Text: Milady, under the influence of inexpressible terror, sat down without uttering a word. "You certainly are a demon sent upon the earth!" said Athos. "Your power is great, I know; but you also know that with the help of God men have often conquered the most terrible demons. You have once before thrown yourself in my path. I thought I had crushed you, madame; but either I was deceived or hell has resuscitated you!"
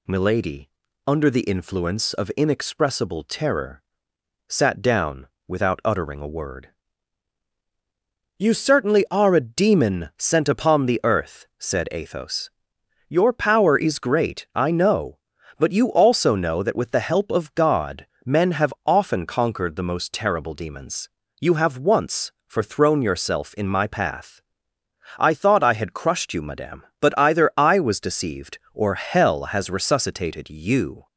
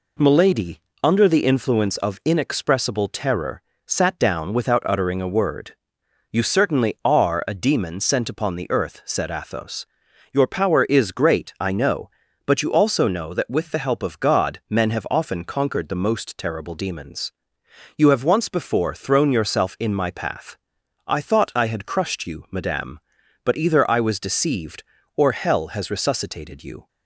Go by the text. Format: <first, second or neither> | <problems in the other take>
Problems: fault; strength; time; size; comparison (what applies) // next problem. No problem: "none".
second | pauses between "down" and "without"; slight; at 5.2 s; 0.22 s long // pauses between "God" and "men"; slight; at 18.0 s; 0.18 s long // says "for" for "before"; at 22.4 s